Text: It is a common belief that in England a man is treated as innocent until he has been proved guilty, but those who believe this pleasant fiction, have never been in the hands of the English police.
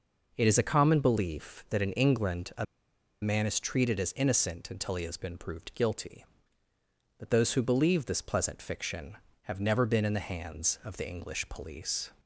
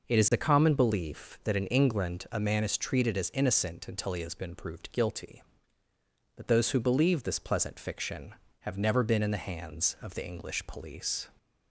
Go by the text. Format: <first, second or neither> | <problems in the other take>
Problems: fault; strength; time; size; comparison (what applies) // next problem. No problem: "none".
second | pauses between "a" and "man"; noticeable; at 2.6 s; 0.57 s long